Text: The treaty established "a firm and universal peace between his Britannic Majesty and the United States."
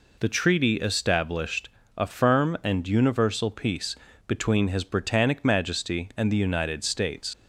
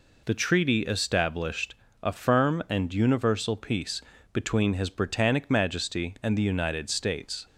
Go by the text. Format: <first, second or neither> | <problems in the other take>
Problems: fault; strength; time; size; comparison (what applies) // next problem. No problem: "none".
second | pauses between "established" and "a"; slight; at 1.6 s; 0.26 s long; slight in the second // pauses between "peace" and "between"; slight; at 3.9 s; 0.30 s long; slight in the second // leaves "States" unfinished; at 7.3 s; 60 ms